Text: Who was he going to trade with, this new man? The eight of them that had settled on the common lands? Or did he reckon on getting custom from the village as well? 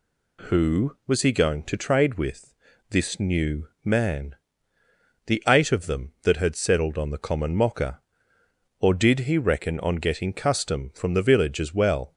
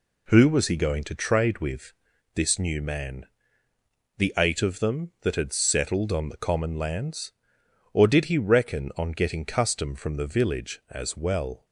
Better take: second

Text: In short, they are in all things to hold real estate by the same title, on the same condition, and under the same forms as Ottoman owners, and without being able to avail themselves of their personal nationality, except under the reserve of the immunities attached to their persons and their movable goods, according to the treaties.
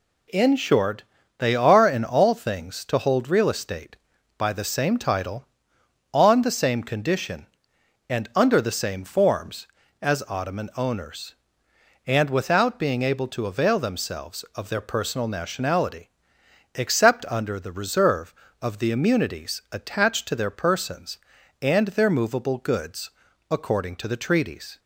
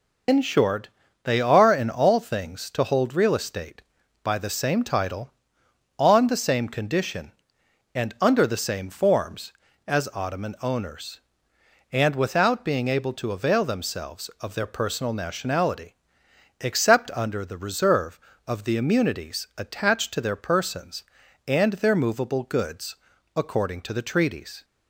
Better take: first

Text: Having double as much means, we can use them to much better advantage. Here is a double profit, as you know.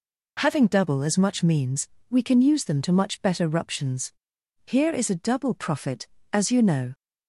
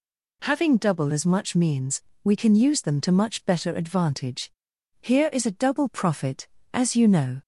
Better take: second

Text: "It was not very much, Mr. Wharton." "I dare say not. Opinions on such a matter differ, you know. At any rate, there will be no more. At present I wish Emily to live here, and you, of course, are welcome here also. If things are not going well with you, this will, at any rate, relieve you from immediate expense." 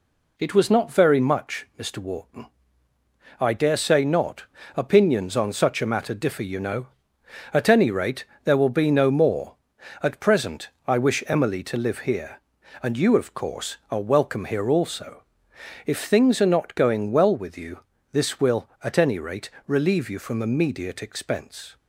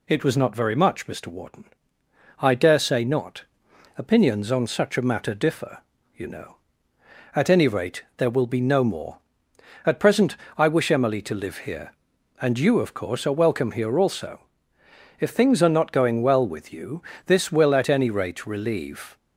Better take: first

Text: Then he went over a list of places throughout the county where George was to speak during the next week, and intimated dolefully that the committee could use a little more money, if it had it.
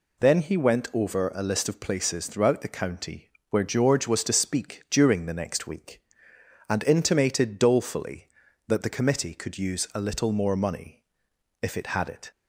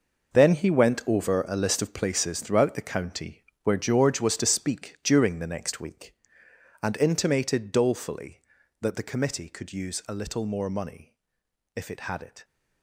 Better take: first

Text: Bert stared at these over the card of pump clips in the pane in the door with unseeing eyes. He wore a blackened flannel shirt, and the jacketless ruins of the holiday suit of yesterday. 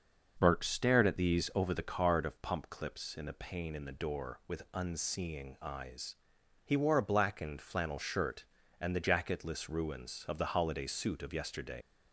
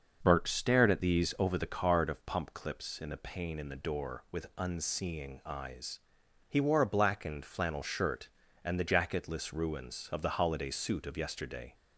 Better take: second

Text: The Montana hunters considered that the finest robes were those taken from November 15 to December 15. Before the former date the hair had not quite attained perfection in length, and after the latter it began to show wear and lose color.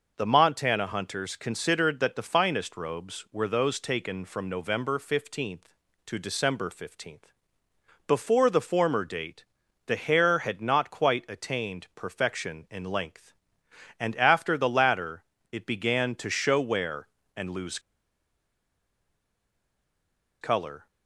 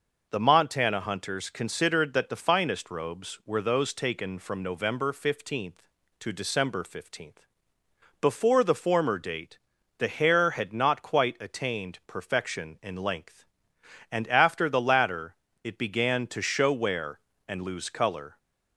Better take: second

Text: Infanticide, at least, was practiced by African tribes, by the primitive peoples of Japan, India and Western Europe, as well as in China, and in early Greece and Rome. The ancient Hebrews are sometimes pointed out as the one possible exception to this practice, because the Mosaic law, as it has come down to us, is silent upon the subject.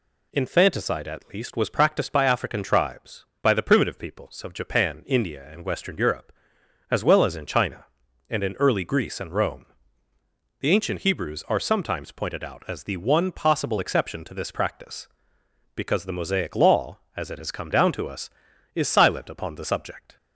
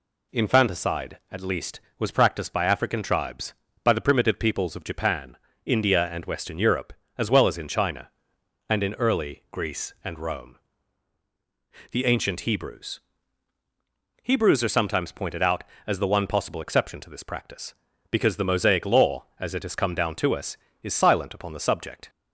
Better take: first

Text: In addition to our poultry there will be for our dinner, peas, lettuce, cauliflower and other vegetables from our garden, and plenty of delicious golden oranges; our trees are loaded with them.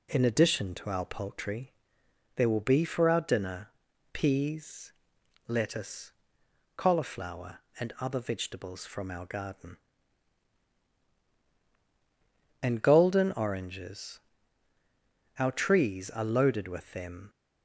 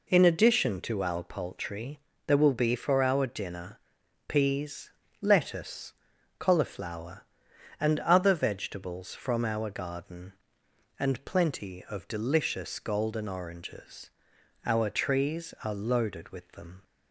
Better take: second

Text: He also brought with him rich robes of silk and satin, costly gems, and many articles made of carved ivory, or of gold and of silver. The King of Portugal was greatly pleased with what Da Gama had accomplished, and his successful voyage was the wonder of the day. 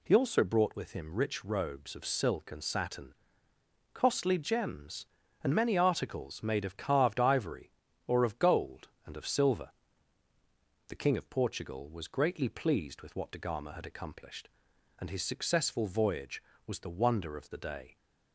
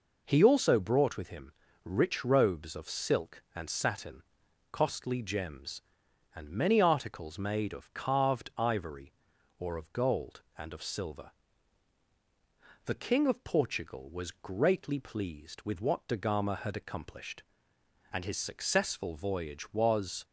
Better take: first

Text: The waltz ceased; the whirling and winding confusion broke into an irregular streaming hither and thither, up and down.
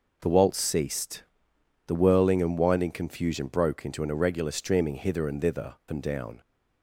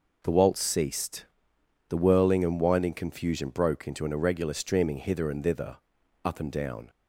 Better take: second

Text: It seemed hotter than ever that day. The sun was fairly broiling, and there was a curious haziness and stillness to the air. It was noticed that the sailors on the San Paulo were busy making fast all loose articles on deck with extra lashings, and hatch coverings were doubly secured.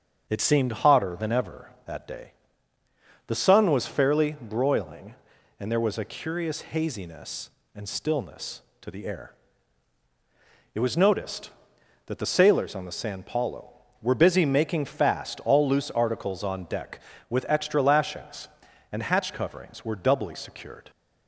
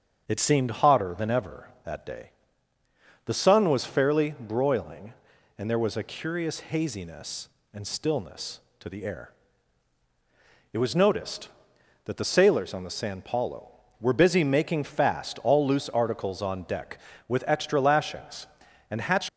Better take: first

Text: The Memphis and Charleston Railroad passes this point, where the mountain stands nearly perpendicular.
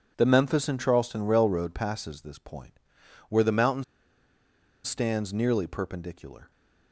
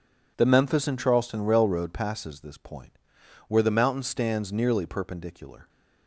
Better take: second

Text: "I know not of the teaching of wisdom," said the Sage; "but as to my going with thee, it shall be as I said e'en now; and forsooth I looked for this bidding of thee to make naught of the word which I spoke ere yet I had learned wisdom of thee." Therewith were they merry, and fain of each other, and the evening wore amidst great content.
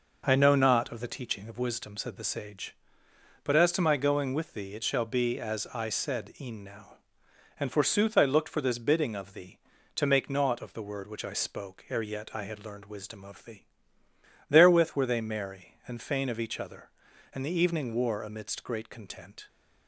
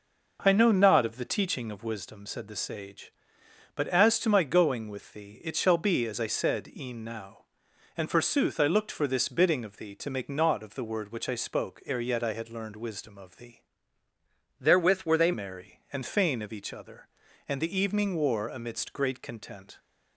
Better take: first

